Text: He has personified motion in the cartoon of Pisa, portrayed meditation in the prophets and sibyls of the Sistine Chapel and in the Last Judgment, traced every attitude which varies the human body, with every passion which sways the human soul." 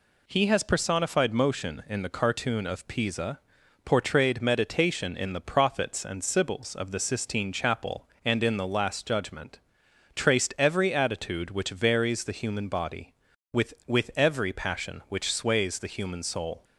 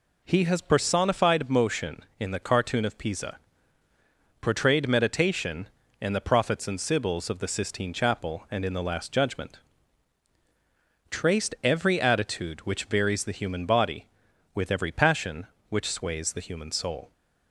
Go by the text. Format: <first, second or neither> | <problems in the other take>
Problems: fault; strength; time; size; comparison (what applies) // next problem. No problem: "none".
second | says "with" twice; at 13.8 s